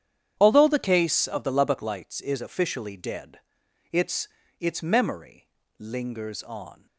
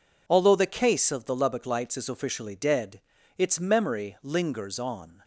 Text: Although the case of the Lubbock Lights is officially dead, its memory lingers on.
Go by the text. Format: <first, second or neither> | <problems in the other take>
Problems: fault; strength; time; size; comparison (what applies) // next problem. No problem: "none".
second | starts louder than the rest; strong; until 1.3 s; 9 dB // says "its" twice; at 4.5 s // pauses between "memory" and "lingers"; slight; at 5.4 s; 0.30 s long